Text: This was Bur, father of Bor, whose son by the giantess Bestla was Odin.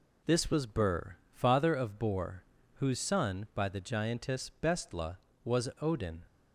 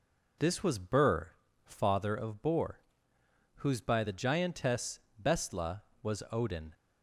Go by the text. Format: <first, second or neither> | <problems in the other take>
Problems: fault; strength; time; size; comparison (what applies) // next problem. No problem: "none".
first | skips "son"; at 3.8 s // pauses between "giantess" and "Bestla"; slight; at 4.9 s; 0.20 s long